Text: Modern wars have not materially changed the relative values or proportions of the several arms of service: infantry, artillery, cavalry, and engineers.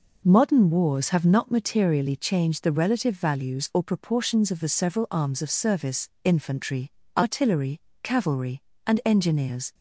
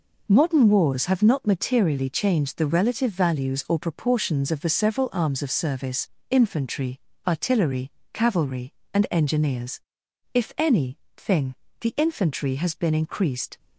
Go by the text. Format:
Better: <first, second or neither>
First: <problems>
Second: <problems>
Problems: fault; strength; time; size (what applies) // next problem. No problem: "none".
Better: first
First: none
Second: goes on to say "If any thing the infantry has been increased"; strong; from 10.3 s on; 3.2 s long